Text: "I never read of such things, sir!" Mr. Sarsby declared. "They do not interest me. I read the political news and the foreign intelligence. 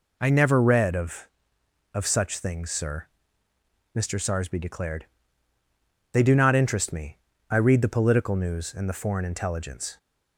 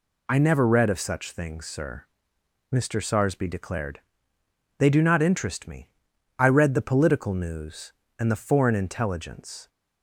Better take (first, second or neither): second